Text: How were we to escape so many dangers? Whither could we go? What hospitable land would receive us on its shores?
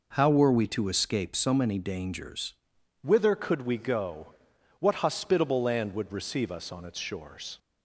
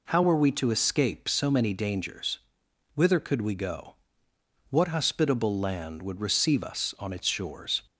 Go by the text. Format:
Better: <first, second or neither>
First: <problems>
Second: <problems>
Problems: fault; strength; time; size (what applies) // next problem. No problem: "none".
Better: second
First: changes voice at "Whither"; from 3.0 s on; 4.5 s long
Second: none